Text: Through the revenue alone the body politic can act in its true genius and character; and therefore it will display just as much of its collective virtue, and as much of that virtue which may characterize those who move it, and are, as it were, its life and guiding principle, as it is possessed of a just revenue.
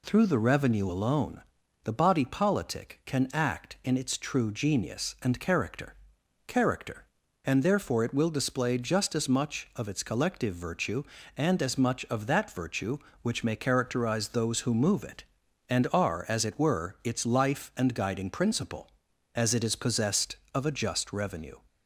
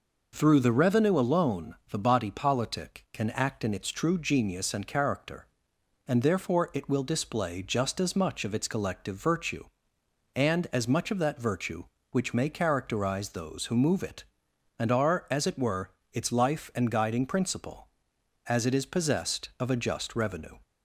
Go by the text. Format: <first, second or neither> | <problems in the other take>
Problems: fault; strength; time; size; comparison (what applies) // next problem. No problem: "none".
second | pauses between "alone" and "the"; at 1.4 s; 0.42 s long // says "character" twice; at 6.4 s